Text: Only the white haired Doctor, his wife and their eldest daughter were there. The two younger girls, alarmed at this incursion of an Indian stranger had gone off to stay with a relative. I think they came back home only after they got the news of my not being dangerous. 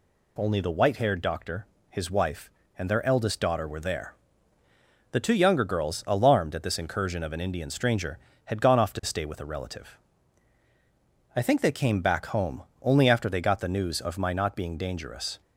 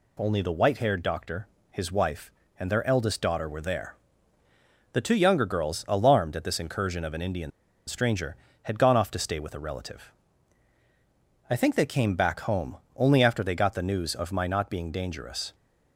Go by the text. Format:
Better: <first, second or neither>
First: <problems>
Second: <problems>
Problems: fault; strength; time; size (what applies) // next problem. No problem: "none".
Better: first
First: pauses between "home" and "only"; slight; at 12.6 s; 0.20 s long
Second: pauses between "Indian" and "stranger"; at 7.5 s; 0.38 s long // pauses between "home" and "only"; slight; at 12.7 s; 0.20 s long